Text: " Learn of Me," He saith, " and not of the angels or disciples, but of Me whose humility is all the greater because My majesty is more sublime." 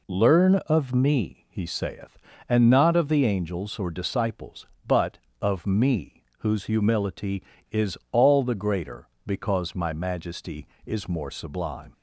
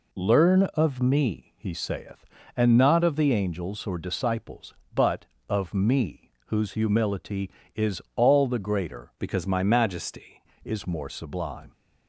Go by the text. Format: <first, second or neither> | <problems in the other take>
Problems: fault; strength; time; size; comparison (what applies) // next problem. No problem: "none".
first | pauses between "Me" and "whose"; slight; at 6.2 s; 0.20 s long; slight in the first // changes voice from "because" to "majesty"; from 9.1 to 10.4 s; 1.3 s long